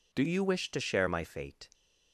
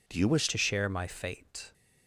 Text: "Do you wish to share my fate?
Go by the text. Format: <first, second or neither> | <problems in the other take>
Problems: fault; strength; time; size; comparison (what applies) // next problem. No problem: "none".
first | changes voice at "to"; from 0.4 s on; 1.3 s long